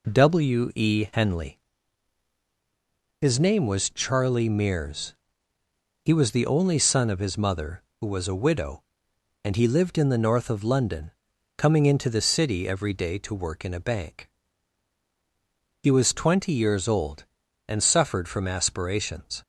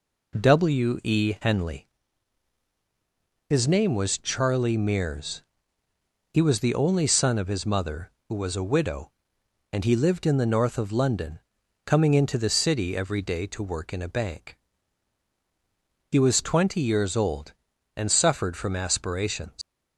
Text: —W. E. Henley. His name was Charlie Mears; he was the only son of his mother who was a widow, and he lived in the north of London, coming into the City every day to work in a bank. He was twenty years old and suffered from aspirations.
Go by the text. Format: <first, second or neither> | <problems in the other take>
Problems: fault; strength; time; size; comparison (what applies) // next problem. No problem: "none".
first | leaves "aspirations" unfinished; at 19.6 s; 85 ms